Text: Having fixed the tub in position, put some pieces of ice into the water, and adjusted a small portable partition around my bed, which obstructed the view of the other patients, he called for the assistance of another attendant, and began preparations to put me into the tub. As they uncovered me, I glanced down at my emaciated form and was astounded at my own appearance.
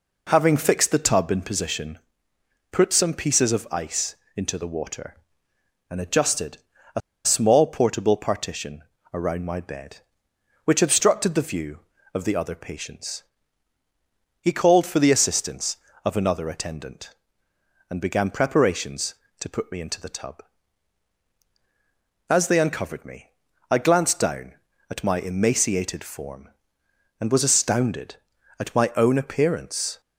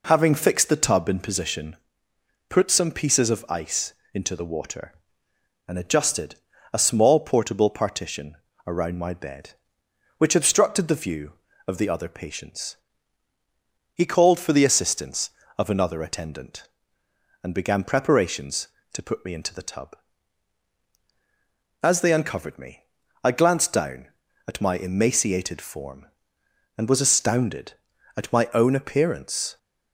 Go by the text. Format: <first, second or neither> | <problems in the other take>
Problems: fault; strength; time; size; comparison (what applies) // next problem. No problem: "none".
second | pauses between "ice" and "into"; slight; at 4.1 s; 0.20 s long; slight in the second // pauses between "adjusted" and "a"; slight; at 6.5 s; 0.36 s long; slight in the second // pauses between "a" and "small"; slight; at 6.9 s; 0.25 s long // pauses between "partition" and "around"; slight; at 8.8 s; 0.32 s long; slight in the second